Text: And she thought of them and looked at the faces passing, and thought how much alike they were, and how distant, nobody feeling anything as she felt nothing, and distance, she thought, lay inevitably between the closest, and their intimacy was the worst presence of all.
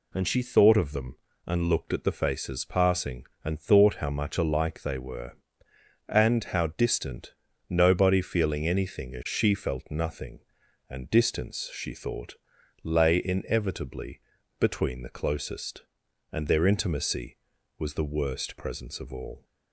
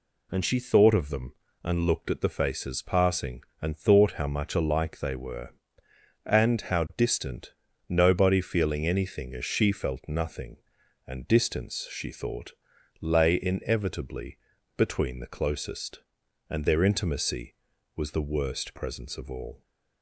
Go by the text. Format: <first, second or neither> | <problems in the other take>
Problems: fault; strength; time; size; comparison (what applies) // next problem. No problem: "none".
neither | pauses between "inevitably" and "between"; the same in both